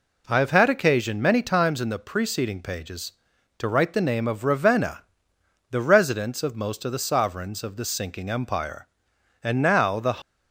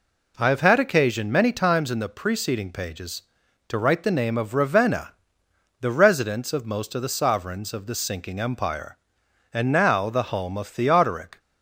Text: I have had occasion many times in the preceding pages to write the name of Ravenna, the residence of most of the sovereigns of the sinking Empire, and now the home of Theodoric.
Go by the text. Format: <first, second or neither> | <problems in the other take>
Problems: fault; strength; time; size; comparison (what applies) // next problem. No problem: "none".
second | stops before "home of Theodoric"; at 10.2 s